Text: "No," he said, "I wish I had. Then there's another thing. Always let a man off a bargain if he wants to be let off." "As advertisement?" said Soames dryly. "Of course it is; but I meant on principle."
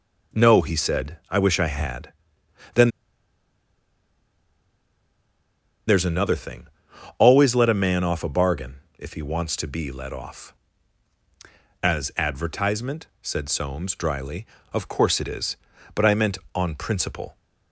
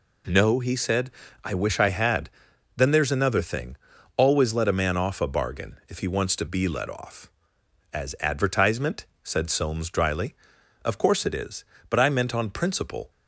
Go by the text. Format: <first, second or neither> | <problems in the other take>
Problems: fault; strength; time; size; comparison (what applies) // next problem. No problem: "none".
second | pauses between "Then" and "there's"; strong; at 2.8 s; 2.9 s long // pauses between "bargain" and "if"; slight; at 8.7 s; 0.18 s long